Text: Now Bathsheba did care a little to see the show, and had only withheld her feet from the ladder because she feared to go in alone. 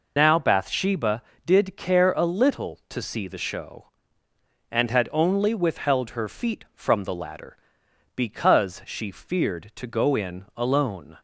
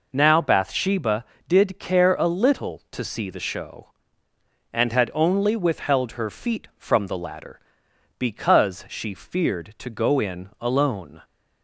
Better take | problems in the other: second | loses the start of "Now"; at 0.1 s; 65 ms

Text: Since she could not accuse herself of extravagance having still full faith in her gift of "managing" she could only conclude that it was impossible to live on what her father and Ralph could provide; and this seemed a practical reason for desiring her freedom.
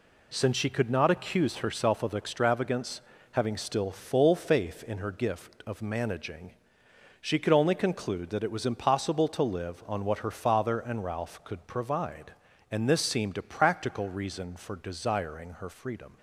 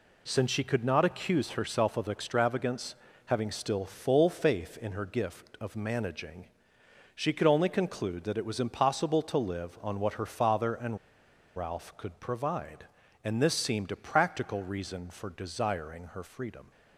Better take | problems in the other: first | pauses between "extravagance" and "having"; slight; at 2.9 s; 0.30 s long; slight in the first // pauses between "managing" and "she"; noticeable; at 6.4 s; 0.66 s long; noticeable in the first // pauses between "and" and "Ralph"; noticeable; at 10.9 s; 0.58 s long

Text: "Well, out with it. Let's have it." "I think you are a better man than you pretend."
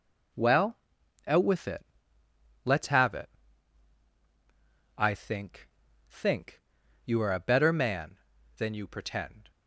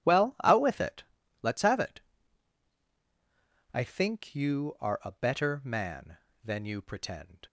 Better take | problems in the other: second | says "think" twice; at 6.0 s

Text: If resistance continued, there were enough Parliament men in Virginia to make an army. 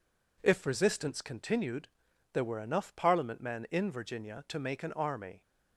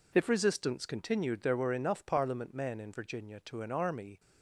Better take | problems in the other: first | skips "make"; at 3.6 s

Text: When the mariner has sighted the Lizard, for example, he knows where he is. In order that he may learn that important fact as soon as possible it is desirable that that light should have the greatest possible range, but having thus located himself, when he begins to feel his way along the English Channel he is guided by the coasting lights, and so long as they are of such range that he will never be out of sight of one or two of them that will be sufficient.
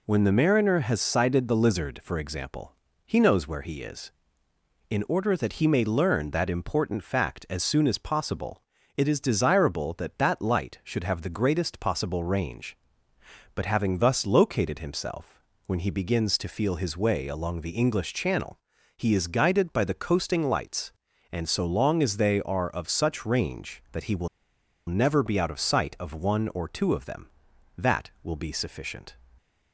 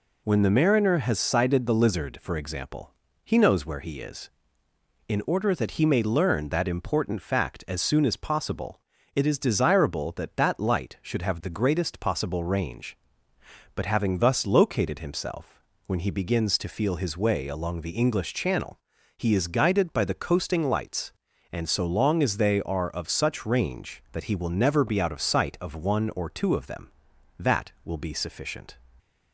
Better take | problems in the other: second | pauses between "possible" and "it"; slight; at 8.6 s; 0.34 s long; slight in the second // pauses between "Channel" and "he"; at 18.5 s; 0.38 s long; also in the second // pauses between "will" and "never"; noticeable; at 24.2 s; 0.61 s long

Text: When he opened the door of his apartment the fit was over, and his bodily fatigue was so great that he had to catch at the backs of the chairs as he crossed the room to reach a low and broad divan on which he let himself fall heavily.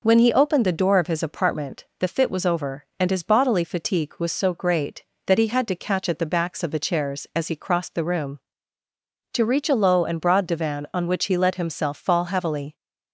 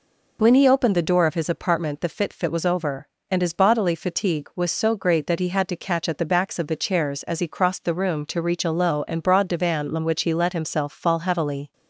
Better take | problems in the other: first | says "fit" twice; at 2.3 s

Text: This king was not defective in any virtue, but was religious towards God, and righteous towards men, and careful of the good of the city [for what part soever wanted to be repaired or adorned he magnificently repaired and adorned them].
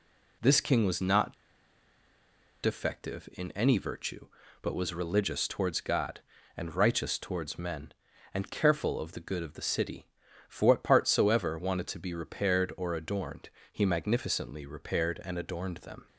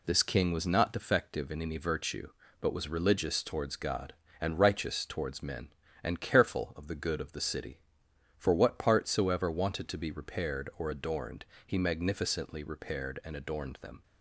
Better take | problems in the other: second | pauses between "not" and "defective"; strong; at 1.3 s; 1.2 s long // pauses between "adorned" and "he"; slight; at 13.4 s; 0.24 s long; slight in the second

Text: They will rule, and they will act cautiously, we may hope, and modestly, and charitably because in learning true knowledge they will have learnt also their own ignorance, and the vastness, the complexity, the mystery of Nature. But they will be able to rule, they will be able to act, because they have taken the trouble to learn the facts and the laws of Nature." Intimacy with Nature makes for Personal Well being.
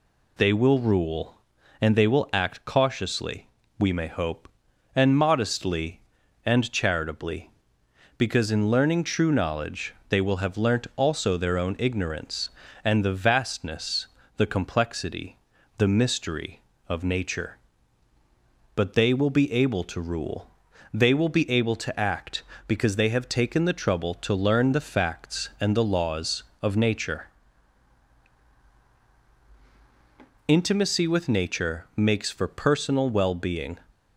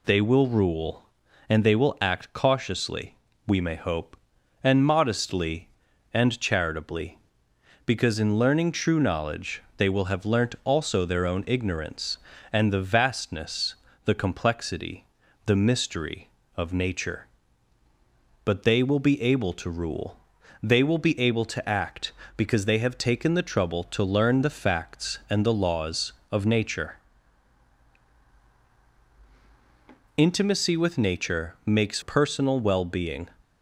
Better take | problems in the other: first | pauses between "knowledge" and "they"; slight; at 9.6 s; 0.16 s long; slight in the first // skips "for"; at 32.0 s

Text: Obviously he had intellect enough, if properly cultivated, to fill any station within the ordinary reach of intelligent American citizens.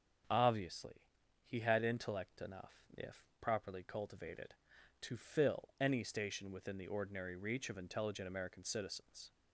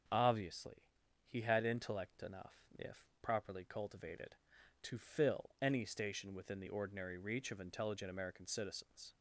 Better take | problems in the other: neither | starts louder than the rest; strong; the same in both // pauses between "Obviously" and "he"; the same in both

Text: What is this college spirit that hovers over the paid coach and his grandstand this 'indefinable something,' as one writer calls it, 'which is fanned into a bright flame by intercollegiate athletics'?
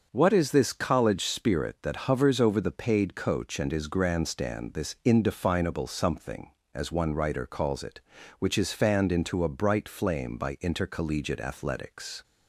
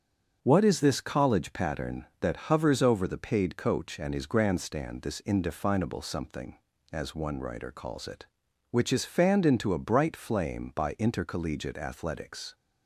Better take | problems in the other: first | starts louder than the rest; until 1.4 s; 6.5 dB; also in the first // says "pattern" for "spirit"; at 1.5 s

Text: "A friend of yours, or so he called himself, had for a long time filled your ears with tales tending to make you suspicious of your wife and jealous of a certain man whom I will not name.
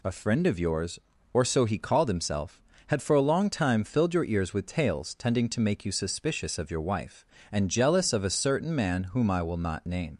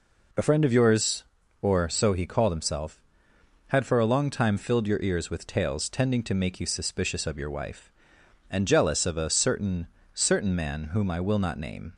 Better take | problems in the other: first | says "certain" twice; at 10.1 s

